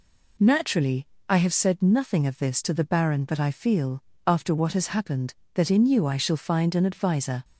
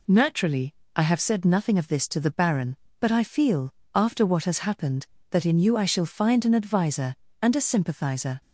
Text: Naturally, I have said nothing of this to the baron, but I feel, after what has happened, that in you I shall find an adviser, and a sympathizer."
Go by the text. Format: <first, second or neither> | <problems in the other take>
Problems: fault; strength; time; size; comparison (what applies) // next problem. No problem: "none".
second | stops before "and a sympathizer"; at 7.4 s